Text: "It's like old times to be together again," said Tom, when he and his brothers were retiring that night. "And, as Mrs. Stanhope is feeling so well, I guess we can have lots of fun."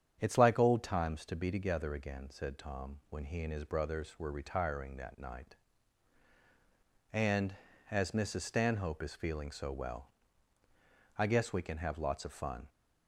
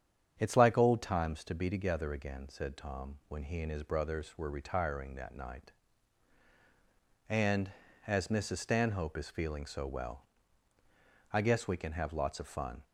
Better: neither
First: starts louder than the rest; strong; until 1.2 s; 8.5 dB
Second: starts louder than the rest; strong; until 1.3 s; 8.5 dB

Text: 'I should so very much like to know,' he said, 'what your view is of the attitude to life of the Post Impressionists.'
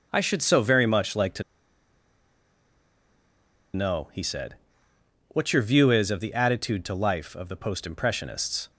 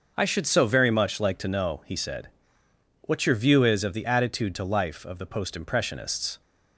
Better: second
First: starts louder than the rest; until 1.1 s; 6 dB // pauses between "to" and "know"; strong; at 1.4 s; 2.3 s long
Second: starts louder than the rest; until 1.1 s; 6 dB

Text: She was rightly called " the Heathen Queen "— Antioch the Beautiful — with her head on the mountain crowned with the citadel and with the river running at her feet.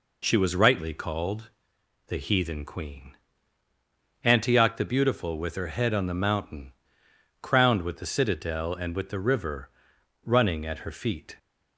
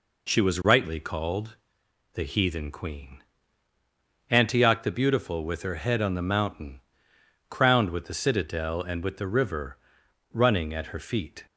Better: neither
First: pauses between "mountain" and "crowned"; noticeable; at 6.7 s; 0.68 s long // pauses between "river" and "running"; noticeable; at 9.7 s; 0.52 s long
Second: pauses between "mountain" and "crowned"; noticeable; at 6.8 s; 0.68 s long // pauses between "river" and "running"; noticeable; at 9.7 s; 0.52 s long

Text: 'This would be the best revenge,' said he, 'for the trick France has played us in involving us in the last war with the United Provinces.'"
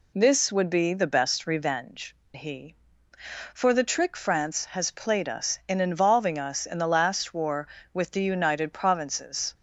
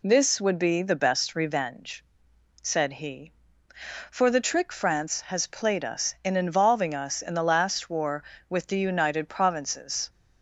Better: second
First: skips "said"; at 2.2 s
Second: none

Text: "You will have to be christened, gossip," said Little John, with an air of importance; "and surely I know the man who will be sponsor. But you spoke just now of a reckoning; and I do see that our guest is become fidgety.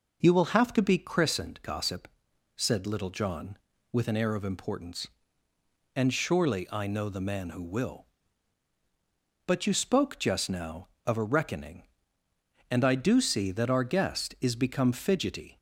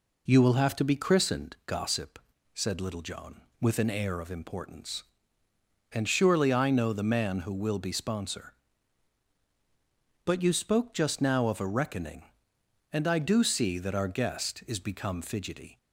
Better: second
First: skips "be sponsor"; at 8.7 s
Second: none

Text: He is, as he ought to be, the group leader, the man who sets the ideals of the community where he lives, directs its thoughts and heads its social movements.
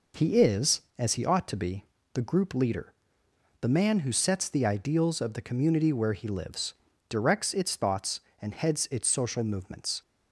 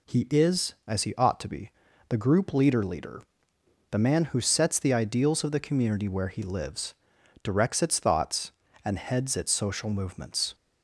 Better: first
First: none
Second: says "leader" twice; at 2.8 s

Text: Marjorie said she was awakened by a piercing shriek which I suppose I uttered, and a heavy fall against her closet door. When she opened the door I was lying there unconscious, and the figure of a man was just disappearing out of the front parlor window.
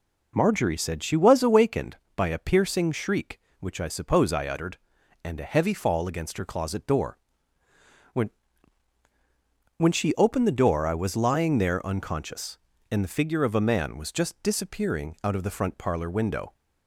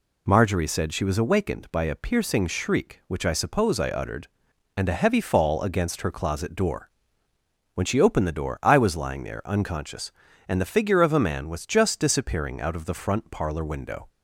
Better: second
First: says "When" twice; at 9.7 s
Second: none

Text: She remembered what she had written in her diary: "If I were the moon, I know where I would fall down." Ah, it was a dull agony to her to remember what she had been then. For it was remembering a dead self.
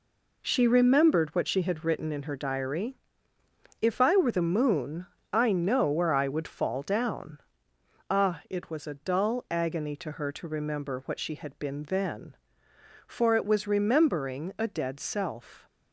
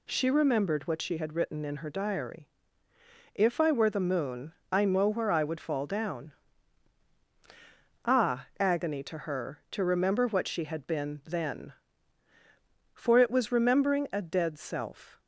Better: first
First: none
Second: skips "it was a dull"; at 8.5 s

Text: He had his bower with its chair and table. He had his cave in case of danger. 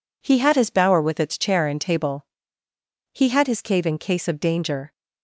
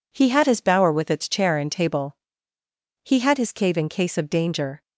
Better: neither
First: none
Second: none

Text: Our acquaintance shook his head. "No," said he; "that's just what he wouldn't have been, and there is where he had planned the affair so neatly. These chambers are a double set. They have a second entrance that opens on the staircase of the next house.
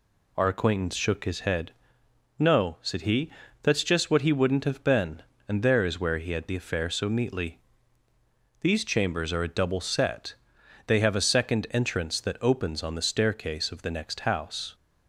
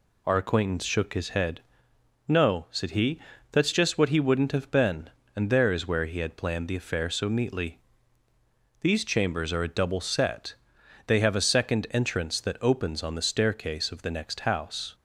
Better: second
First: skips "planned"; at 6.4 s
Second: none

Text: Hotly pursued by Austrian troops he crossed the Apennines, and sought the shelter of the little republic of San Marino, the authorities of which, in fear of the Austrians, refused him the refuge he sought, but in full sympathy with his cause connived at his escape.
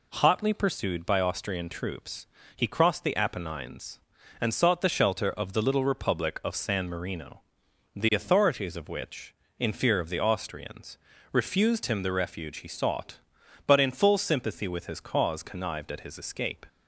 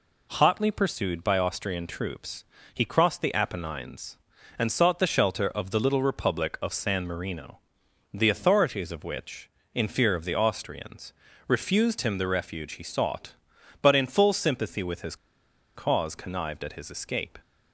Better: first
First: pauses between "troops" and "he"; slight; at 2.2 s; 0.30 s long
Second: pauses between "troops" and "he"; slight; at 2.4 s; 0.30 s long // pauses between "his" and "cause"; noticeable; at 15.1 s; 0.59 s long

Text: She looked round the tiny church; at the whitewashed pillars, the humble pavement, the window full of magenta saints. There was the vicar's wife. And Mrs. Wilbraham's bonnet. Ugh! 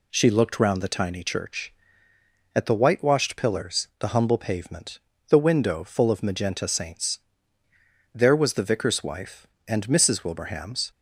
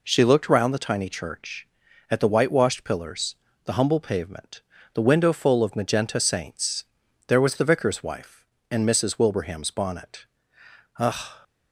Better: second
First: stops before "bonnet Ugh"; at 10.9 s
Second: none

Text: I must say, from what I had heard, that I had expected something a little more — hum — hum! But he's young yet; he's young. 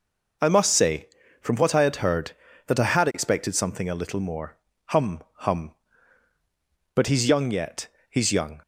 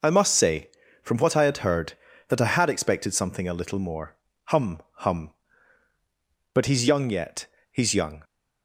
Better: neither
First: none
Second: none

